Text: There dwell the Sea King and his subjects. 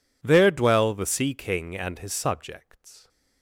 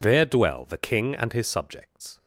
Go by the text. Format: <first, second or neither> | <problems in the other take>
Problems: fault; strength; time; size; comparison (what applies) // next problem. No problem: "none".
first | skips "Sea"; at 0.7 s